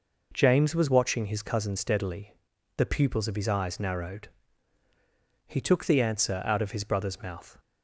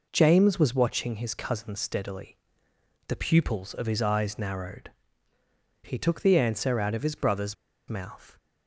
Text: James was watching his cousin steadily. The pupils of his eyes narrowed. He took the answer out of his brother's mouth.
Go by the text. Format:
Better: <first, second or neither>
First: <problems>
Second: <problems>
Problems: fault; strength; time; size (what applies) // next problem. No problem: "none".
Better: first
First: none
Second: pauses between "brother's" and "mouth"; slight; at 7.5 s; 0.34 s long